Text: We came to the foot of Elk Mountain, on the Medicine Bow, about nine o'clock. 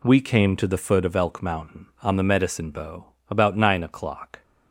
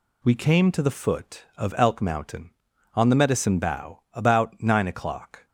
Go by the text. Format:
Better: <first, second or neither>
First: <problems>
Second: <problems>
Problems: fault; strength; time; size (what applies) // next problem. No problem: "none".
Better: neither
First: none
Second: none